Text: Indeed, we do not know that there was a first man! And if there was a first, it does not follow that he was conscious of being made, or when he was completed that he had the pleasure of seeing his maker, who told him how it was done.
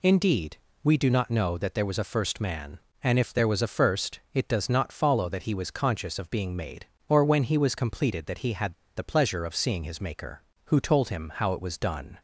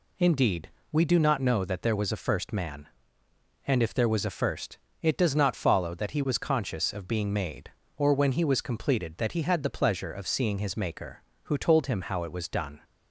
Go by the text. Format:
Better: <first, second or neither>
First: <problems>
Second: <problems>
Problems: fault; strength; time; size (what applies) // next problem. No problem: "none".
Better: second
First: pauses between "had" and "the"; slight; at 8.7 s; 0.24 s long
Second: none